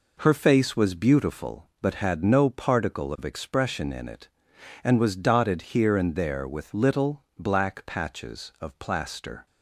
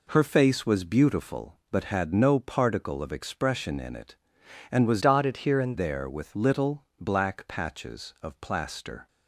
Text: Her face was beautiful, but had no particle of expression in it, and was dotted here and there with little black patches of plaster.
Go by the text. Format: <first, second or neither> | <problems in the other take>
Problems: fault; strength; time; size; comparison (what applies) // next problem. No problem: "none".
first | changes voice from "dotted" to "and"; from 5.0 to 5.7 s; 0.7 s long